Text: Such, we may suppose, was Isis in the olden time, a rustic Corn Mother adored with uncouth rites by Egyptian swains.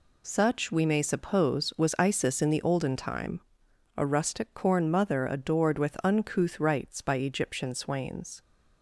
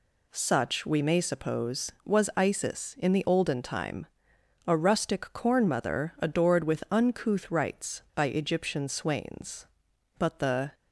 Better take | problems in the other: first | goes on to say "But the"; from 10.1 s on; 0.54 s long

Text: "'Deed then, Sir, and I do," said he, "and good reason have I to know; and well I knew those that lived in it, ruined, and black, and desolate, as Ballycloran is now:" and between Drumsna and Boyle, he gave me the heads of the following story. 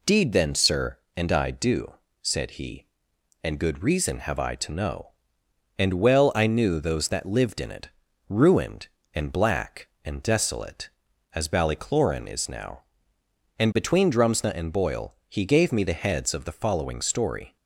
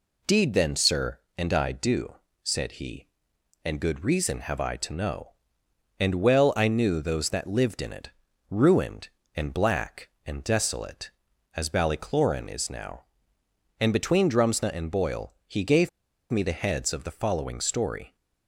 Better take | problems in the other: first | pauses between "gave" and "me"; at 15.8 s; 0.41 s long

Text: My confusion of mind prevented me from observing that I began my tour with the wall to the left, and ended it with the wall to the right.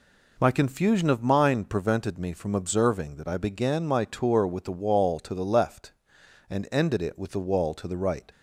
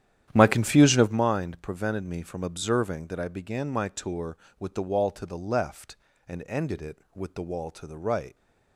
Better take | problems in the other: first | starts louder than the rest; strong; until 1.3 s; 10.5 dB

